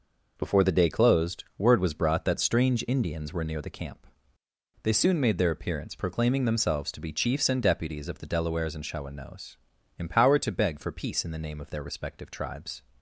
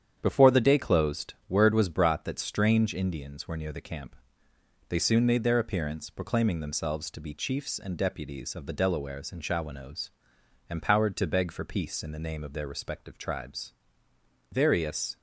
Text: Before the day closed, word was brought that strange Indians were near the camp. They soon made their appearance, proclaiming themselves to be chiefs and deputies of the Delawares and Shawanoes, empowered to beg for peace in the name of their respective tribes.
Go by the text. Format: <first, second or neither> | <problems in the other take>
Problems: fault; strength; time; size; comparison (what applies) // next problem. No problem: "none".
first | starts louder than the rest; strong; until 1.2 s; 8.5 dB // goes on to say "Various"; noticeable; from 14.5 s on; 0.66 s long